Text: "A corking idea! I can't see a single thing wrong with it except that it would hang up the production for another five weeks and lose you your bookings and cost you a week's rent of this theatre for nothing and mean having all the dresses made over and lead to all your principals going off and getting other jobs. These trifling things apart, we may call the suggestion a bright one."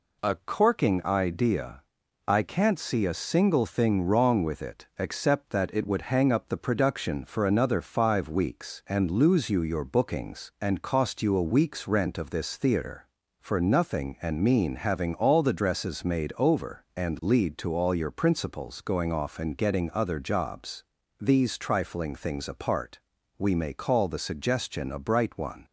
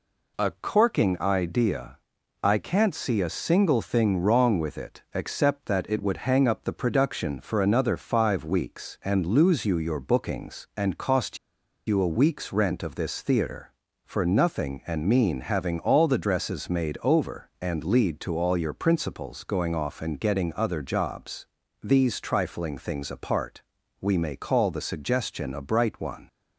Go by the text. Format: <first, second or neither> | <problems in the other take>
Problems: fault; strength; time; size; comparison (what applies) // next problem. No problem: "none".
first | pauses between "cost" and "you"; noticeable; at 11.3 s; 0.50 s long